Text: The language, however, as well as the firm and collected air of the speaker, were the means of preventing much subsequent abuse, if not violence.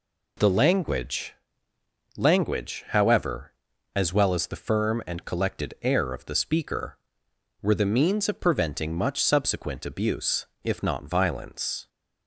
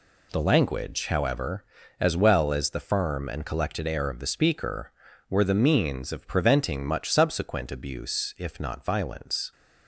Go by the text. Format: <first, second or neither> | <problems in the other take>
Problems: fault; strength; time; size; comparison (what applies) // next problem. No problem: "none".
second | says "language" twice; at 2.1 s